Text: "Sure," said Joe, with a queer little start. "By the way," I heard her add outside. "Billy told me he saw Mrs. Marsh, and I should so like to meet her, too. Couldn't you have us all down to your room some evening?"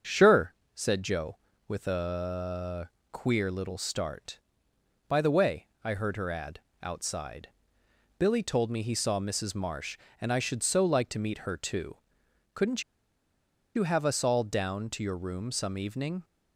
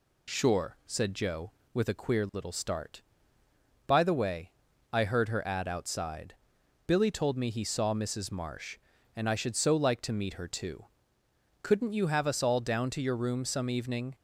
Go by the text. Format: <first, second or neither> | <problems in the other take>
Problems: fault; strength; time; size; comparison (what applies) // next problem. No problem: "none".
second | starts louder than the rest; until 1.3 s; 6.5 dB // pauses between "a" and "queer"; slight; at 2.8 s; 0.20 s long // pauses between "add" and "outside"; slight; at 6.5 s; 0.20 s long // pauses between "Couldn't" and "you"; noticeable; at 12.8 s; 0.93 s long